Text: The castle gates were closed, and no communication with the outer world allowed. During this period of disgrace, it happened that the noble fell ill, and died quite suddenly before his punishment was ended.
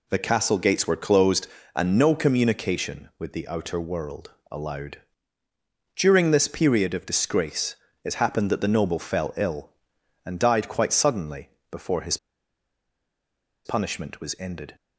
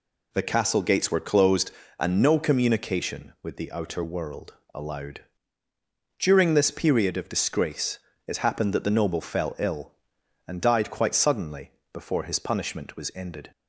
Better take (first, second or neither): second